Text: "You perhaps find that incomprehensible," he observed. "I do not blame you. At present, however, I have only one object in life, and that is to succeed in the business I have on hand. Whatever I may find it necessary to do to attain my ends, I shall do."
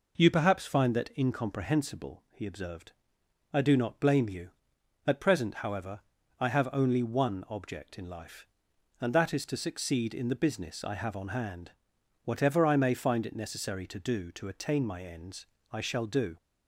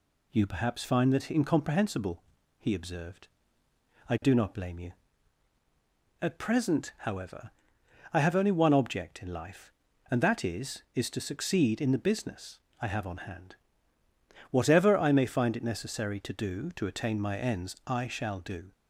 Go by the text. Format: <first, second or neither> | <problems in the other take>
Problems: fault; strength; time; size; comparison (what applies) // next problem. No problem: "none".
first | says "is" twice; at 10.9 s // pauses between "business" and "I"; slight; at 12.5 s; 0.22 s long